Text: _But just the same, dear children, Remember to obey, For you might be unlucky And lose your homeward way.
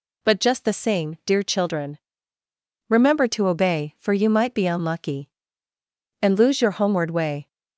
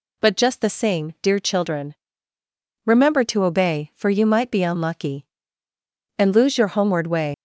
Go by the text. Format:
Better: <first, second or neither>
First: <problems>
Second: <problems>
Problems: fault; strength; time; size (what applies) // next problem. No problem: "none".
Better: first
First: none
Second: leaves "way" unfinished; at 7.3 s; 95 ms